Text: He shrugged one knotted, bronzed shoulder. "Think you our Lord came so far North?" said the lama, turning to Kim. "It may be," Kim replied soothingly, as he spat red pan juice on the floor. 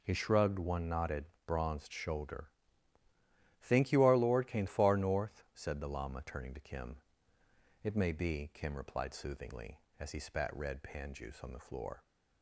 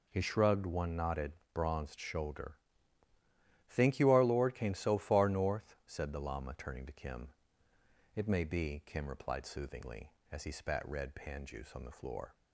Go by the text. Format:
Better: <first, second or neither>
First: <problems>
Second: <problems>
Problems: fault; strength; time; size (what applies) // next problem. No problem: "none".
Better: second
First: skips "so"; at 4.6 s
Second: none